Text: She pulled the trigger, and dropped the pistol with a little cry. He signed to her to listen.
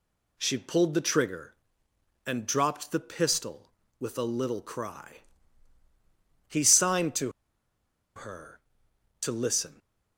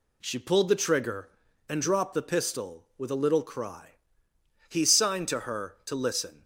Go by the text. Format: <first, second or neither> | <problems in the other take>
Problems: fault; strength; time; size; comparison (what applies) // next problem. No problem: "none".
second | pauses between "to" and "her"; noticeable; at 7.3 s; 0.84 s long